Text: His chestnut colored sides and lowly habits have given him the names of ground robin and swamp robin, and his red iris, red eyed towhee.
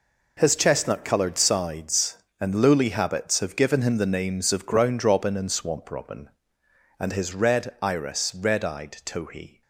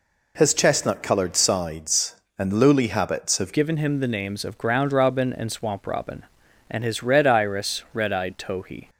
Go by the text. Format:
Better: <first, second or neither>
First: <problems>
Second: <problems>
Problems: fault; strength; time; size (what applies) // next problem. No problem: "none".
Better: first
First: none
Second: changes voice at "given"; from 3.5 s on; 5.3 s long